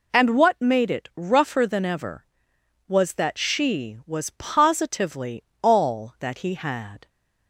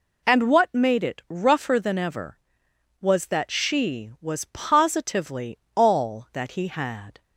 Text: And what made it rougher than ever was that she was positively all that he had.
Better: neither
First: pauses between "positively" and "all"; slight; at 5.4 s; 0.20 s long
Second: pauses between "positively" and "all"; slight; at 5.5 s; 0.18 s long

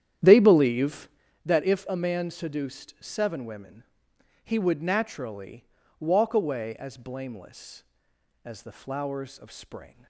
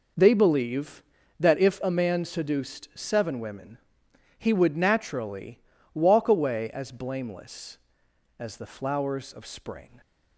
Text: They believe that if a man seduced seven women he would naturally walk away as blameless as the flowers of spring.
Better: second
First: starts louder than the rest; strong; until 1.2 s; 10.5 dB // pauses between "women" and "he"; noticeable; at 3.8 s; 0.60 s long // pauses between "naturally" and "walk"; slight; at 5.6 s; 0.36 s long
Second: pauses between "women" and "he"; noticeable; at 3.7 s; 0.60 s long // pauses between "naturally" and "walk"; slight; at 5.5 s; 0.36 s long

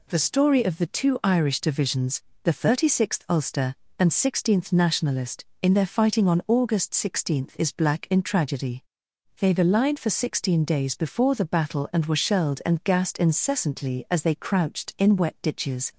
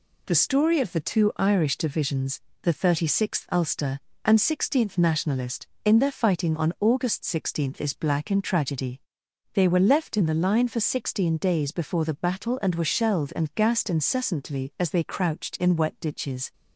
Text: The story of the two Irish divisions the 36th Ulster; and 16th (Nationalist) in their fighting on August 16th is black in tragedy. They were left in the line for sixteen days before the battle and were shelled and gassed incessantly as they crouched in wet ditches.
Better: second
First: pauses between "divisions" and "the"; slight; at 2.2 s; 0.22 s long // skips "were left in"; at 9.5 s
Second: pauses between "divisions" and "the"; slight; at 2.4 s; 0.22 s long

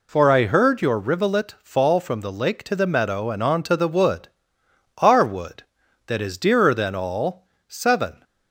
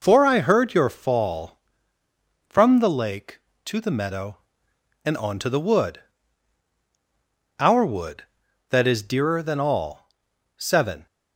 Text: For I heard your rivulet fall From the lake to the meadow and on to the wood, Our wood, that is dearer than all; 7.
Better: first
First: none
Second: skips "rivulet"; at 0.8 s

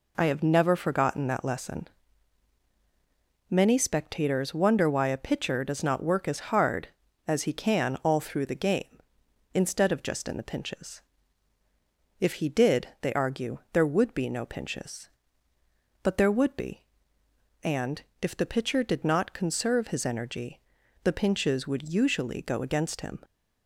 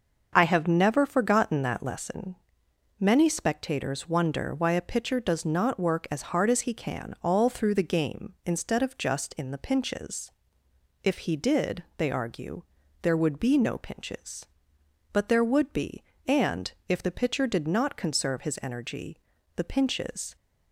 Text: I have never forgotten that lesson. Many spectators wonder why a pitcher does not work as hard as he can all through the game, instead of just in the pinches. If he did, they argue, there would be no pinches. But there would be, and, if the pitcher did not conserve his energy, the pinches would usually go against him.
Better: first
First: none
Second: starts louder than the rest; until 1.3 s; 6 dB // stops before "would usually go against him"; at 20.3 s

